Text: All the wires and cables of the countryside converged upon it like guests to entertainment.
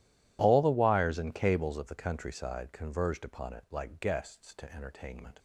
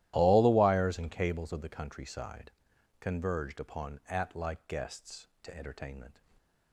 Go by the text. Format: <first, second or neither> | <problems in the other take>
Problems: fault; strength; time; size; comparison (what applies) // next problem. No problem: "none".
first | starts louder than the rest; strong; until 1.1 s; 14 dB // pauses between "countryside" and "converged"; noticeable; at 2.5 s; 0.48 s long // says "at" for "it"; at 4.0 s